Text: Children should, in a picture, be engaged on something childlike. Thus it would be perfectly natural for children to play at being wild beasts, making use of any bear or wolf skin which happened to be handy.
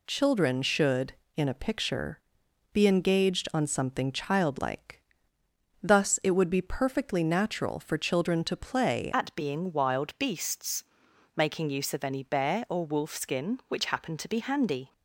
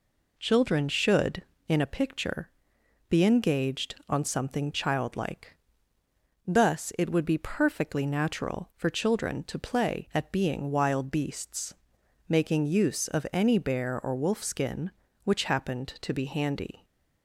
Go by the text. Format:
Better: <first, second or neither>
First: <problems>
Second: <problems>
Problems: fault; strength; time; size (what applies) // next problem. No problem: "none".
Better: second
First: changes voice at "at"; from 9.1 s on; 5.8 s long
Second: none